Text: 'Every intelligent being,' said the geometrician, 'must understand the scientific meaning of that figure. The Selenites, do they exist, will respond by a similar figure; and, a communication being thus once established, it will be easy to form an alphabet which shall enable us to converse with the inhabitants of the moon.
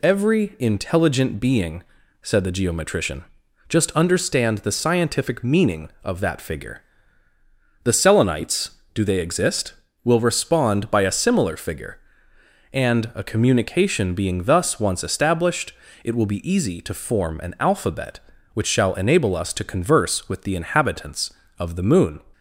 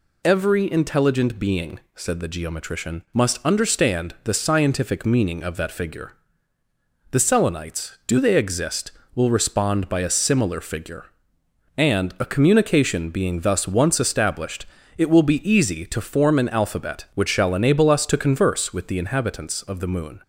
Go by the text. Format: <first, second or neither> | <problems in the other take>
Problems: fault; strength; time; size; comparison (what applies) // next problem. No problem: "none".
second | says "just" for "must"; at 3.6 s